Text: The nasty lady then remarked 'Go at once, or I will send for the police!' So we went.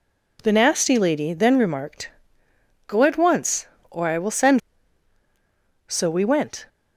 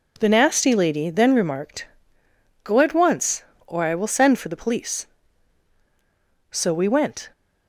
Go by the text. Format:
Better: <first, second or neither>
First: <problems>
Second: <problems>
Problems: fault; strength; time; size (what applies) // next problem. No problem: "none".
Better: second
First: pauses between "remarked" and "Go"; noticeable; at 2.0 s; 0.78 s long // skips "for the police"; at 5.2 s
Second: pauses between "remarked" and "Go"; noticeable; at 1.8 s; 0.78 s long